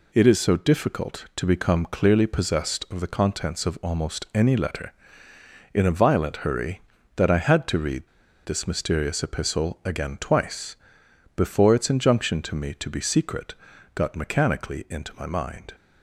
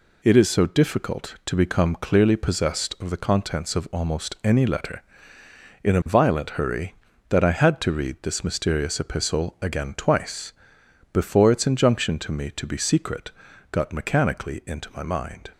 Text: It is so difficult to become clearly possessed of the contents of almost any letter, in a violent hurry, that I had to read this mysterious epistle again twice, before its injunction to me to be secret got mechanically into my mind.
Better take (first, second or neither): second